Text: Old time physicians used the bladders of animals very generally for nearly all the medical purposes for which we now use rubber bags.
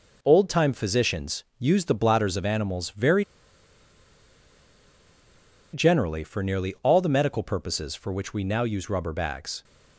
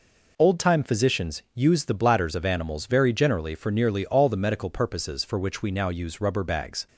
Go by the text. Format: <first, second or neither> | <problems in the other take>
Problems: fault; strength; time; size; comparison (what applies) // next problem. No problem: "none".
second | pauses between "very" and "generally"; strong; at 3.2 s; 2.4 s long